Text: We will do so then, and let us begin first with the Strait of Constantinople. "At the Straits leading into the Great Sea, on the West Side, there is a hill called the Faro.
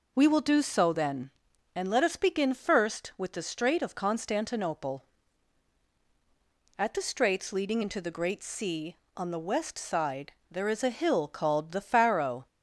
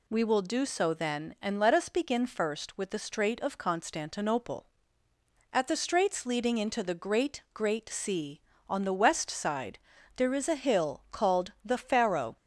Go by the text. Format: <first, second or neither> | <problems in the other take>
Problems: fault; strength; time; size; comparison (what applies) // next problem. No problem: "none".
first | says "Great" twice; at 7.5 s